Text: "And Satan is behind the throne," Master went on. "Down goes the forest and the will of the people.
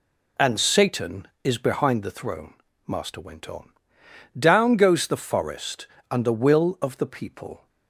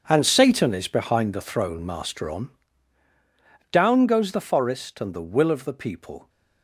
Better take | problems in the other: first | starts louder than the rest; strong; until 1.0 s; 7 dB // skips "went"; at 2.2 s

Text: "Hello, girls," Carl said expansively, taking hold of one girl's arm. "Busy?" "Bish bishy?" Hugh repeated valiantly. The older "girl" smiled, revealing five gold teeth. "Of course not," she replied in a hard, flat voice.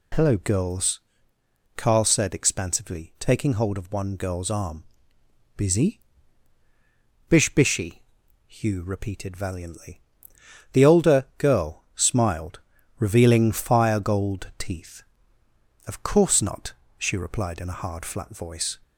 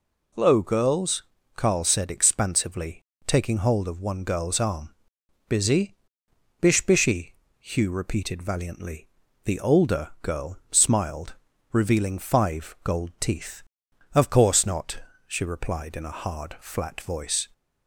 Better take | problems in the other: second | says "fire" for "five"; at 13.5 s

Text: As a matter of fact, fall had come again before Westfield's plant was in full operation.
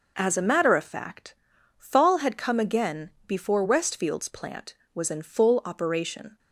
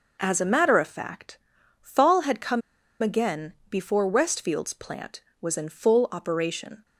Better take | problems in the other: first | pauses between "come" and "again"; at 2.6 s; 0.42 s long // pauses between "again" and "before"; slight; at 3.5 s; 0.16 s long; slight in the first

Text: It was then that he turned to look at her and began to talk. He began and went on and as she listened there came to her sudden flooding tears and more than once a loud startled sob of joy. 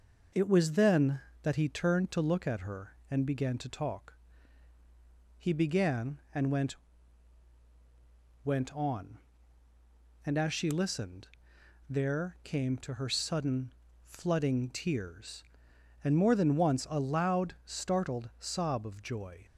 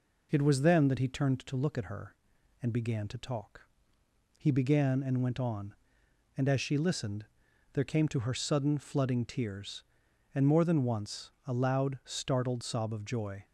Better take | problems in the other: second | says "went" twice; at 8.4 s // pauses between "listened" and "there"; noticeable; at 11.2 s; 0.62 s long; noticeable in the second // pauses between "sudden" and "flooding"; slight; at 13.6 s; 0.34 s long

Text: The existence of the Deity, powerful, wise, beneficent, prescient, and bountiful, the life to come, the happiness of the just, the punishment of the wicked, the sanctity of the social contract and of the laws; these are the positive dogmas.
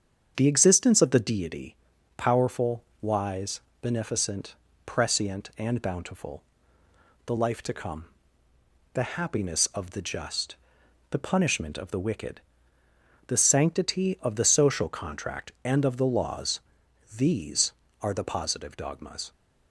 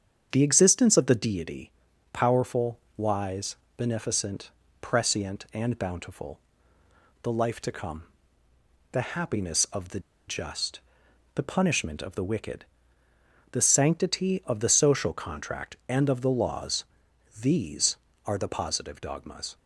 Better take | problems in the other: first | starts louder than the rest; strong; until 1.3 s; 7.5 dB; strong in the first // pauses between "the" and "just"; slight; at 9.9 s; 0.28 s long

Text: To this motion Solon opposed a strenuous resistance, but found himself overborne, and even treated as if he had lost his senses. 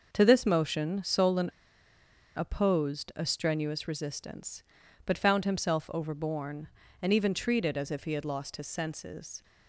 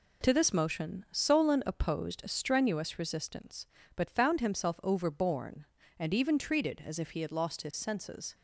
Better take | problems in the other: second | pauses between "Solon" and "opposed"; noticeable; at 1.4 s; 0.88 s long

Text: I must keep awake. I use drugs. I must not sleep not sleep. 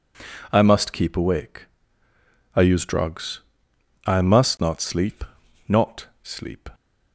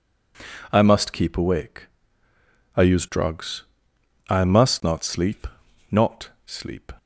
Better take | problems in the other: neither | pauses between "sleep" and "not"; the same in both // pauses between "not" and "sleep"; slight; the same in both

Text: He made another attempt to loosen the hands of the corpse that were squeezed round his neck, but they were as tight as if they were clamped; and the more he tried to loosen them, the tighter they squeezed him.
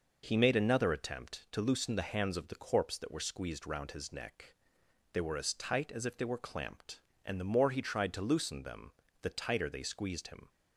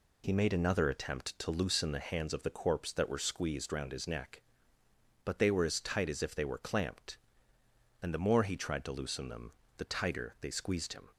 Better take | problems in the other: second | skips "but"; at 4.8 s

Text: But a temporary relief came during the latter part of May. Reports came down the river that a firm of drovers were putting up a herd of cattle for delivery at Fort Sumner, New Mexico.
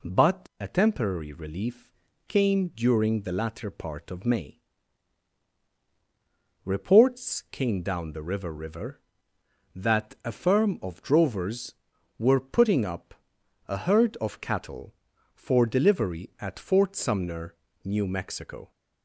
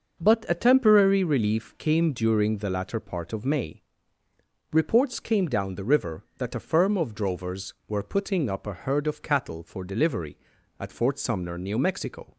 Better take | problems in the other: second | pauses between "relief" and "came"; slight; at 1.9 s; 0.36 s long // says "river" twice; at 8.5 s // pauses between "up" and "a"; noticeable; at 13.1 s; 0.54 s long

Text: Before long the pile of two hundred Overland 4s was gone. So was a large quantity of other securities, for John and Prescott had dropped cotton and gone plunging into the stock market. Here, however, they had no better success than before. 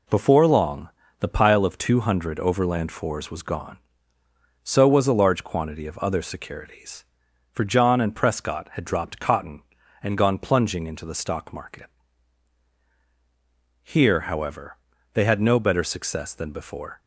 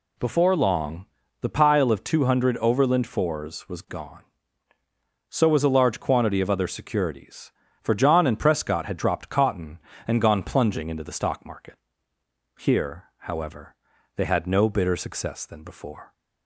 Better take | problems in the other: first | pauses between "long" and "the"; slight; at 1.0 s; 0.36 s long; slight in the first // says "bitter" for "better"; at 14.6 s

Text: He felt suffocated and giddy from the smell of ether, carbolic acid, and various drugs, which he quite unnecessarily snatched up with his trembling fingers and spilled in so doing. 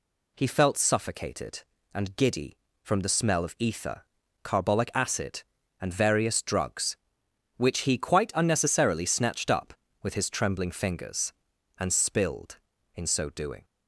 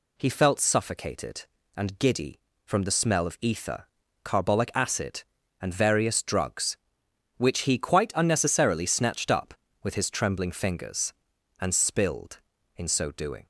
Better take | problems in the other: neither | none

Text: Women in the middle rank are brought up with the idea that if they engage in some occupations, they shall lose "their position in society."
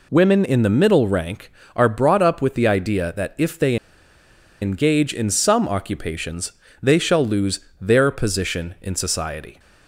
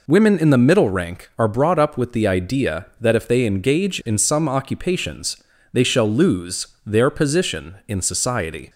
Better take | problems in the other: second | pauses between "they" and "engage"; noticeable; at 3.7 s; 0.86 s long // pauses between "lose" and "their"; slight; at 7.6 s; 0.20 s long; slight in the second

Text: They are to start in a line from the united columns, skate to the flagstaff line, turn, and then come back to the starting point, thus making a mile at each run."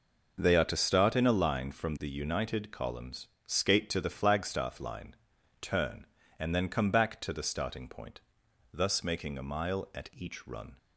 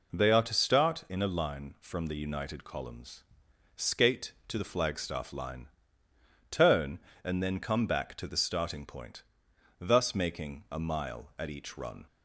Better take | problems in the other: neither | none

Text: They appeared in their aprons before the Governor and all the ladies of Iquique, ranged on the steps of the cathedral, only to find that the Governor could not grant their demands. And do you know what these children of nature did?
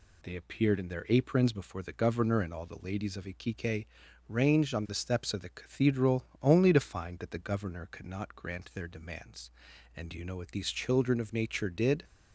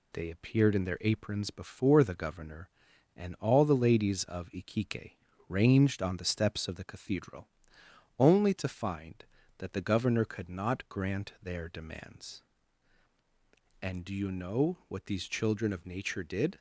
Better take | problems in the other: neither | none

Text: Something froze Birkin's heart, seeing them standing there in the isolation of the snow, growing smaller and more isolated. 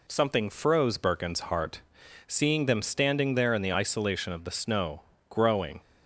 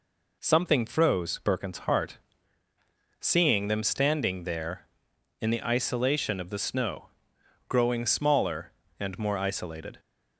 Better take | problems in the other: second | stops before "smaller and more isolated"; at 5.7 s

